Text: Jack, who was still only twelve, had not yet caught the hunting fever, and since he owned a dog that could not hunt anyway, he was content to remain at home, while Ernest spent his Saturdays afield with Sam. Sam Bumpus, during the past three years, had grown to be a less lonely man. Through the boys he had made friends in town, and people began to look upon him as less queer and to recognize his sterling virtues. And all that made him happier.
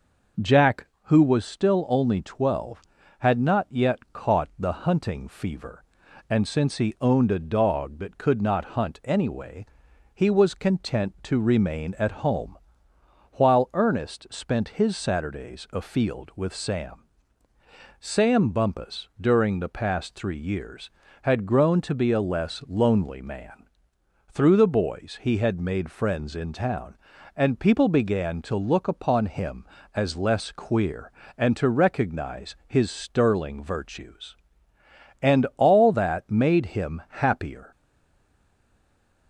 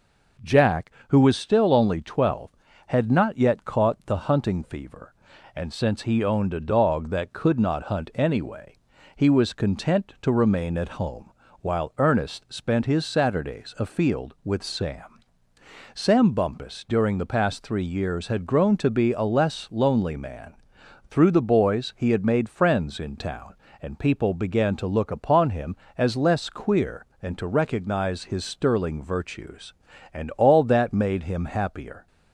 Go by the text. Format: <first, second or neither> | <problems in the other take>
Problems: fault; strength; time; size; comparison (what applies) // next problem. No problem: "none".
second | stays silent after the last word; noticeable; from 37.7 s on; 1.5 s long